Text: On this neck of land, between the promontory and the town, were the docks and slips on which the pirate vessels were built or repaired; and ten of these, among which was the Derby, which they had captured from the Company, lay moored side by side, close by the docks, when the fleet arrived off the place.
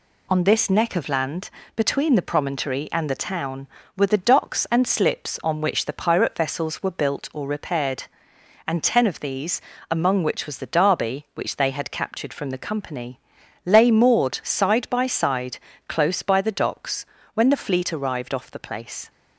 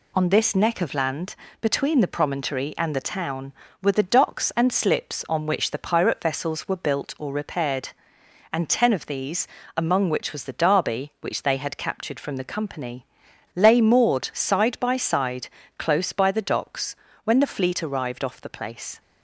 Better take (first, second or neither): neither